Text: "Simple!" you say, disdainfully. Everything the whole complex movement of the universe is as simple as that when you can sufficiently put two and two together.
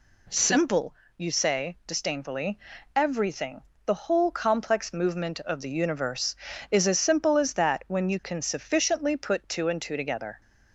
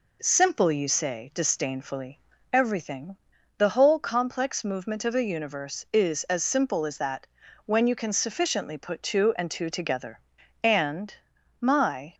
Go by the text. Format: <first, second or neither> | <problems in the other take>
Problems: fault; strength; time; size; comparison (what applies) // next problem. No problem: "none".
first | pauses between "Everything" and "the"; at 3.1 s; 0.40 s long; slight in the first // pauses between "that" and "when"; at 7.2 s; 0.42 s long // goes on to say "And my"; from 10.6 s on; 1.5 s long